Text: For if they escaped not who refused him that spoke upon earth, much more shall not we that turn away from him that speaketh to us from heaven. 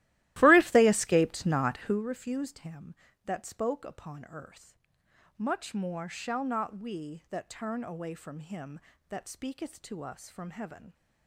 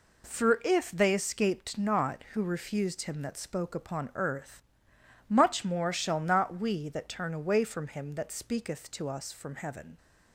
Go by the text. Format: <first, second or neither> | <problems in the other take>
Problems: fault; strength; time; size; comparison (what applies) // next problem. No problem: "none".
second | starts louder than the rest; strong; until 2.0 s; 16 dB